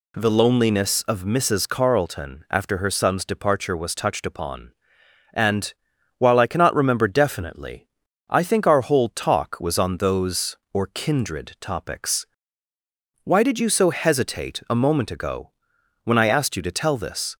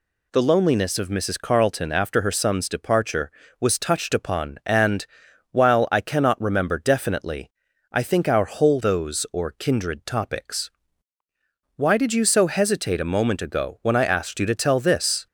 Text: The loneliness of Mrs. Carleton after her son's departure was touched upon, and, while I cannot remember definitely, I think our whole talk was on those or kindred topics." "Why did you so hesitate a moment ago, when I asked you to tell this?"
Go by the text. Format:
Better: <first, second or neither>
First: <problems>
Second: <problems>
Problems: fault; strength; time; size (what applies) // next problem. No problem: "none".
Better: first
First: none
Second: skips "talk was on"; at 8.8 s